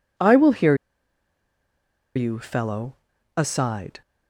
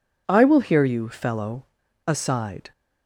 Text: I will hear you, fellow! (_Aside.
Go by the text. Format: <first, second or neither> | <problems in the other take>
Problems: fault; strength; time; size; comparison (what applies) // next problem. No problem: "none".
second | pauses between "hear" and "you"; strong; at 0.7 s; 1.4 s long